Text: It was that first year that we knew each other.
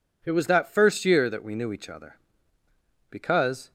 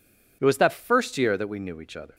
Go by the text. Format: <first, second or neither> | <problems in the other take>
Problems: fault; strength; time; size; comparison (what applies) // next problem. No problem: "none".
second | goes on to say "Because"; noticeable; from 3.1 s on; 0.62 s long